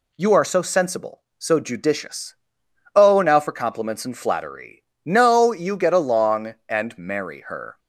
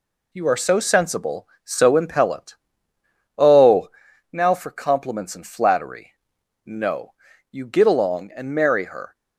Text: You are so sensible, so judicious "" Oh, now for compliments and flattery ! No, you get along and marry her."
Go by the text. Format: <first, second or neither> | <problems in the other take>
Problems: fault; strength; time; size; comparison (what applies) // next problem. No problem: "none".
first | says "impellent" for "judicious"; at 1.9 s